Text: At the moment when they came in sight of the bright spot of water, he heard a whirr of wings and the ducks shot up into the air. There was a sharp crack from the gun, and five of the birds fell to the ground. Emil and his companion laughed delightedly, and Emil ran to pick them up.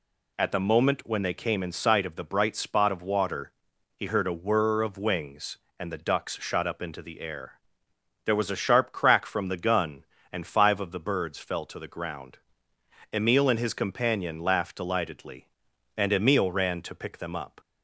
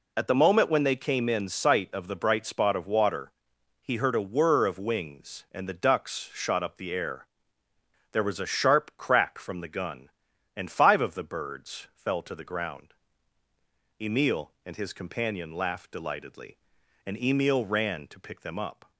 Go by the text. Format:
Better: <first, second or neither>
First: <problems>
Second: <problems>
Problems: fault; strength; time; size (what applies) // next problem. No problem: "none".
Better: first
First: none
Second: skips "into"; at 6.7 s